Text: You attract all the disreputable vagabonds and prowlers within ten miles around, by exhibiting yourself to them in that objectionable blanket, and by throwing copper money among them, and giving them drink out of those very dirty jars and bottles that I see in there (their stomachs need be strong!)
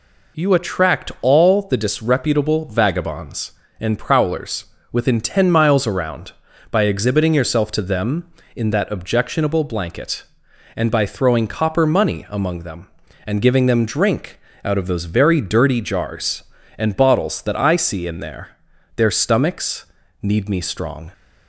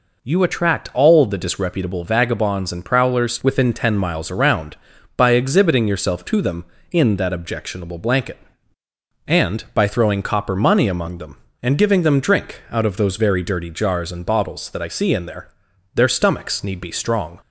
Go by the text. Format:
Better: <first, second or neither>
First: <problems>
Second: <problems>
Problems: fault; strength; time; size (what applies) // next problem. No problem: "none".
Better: second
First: pauses between "prowlers" and "within"; slight; at 4.6 s; 0.26 s long // pauses between "drink" and "out"; slight; at 14.4 s; 0.24 s long // pauses between "stomachs" and "need"; slight; at 19.8 s; 0.36 s long // says "me" for "be"; at 20.4 s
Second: none